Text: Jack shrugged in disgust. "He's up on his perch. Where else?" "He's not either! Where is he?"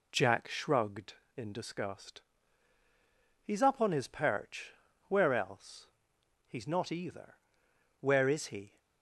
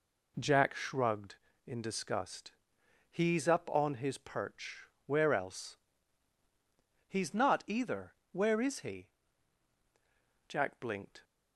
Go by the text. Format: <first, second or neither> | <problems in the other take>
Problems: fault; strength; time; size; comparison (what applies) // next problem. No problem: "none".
first | goes on to say "Jack blinked"; noticeable; from 10.4 s on; 0.74 s long